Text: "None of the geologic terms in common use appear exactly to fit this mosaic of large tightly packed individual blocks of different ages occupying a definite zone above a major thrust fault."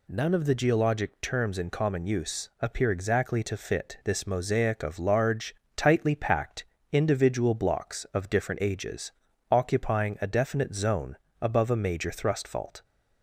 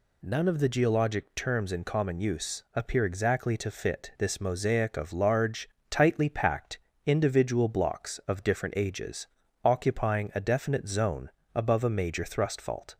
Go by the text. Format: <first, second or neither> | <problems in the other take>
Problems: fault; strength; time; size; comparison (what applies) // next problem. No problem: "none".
neither | pauses between "large" and "tightly"; slight; the same in both // pauses between "packed" and "individual"; slight; the same in both // pauses between "ages" and "occupying"; the same in both // pauses between "zone" and "above"; slight; the same in both